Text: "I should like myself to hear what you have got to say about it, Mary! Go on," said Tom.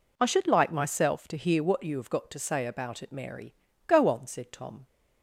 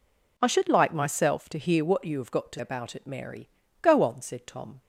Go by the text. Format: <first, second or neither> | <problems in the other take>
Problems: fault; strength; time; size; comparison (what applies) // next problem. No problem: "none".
first | skips "say"; at 2.5 s